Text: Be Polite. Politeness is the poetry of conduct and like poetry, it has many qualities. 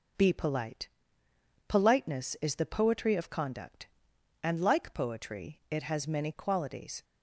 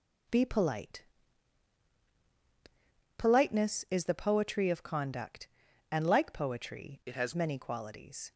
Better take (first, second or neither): first